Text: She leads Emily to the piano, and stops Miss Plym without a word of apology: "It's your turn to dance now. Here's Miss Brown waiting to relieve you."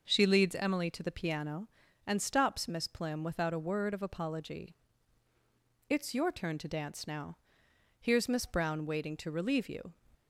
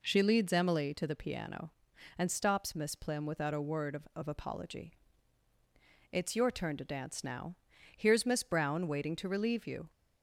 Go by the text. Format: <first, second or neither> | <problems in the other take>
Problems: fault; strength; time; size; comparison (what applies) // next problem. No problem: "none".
first | says "of" twice; at 4.1 s